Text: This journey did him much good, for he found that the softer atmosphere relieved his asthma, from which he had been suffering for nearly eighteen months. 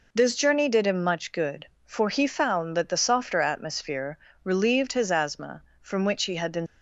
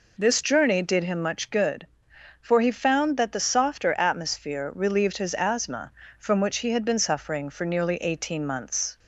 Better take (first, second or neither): second